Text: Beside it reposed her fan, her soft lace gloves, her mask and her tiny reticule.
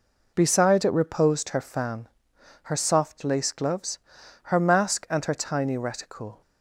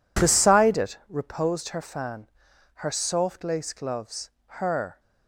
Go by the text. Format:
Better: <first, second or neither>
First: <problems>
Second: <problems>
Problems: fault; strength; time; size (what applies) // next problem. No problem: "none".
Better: first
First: none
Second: stops before "mask and her tiny reticule"; at 4.9 s